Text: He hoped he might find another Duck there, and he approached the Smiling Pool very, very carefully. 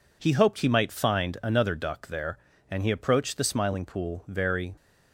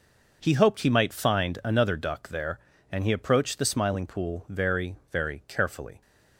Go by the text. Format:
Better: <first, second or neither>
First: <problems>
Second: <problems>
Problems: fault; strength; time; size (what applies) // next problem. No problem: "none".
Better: second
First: stops before "very carefully"; at 4.7 s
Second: none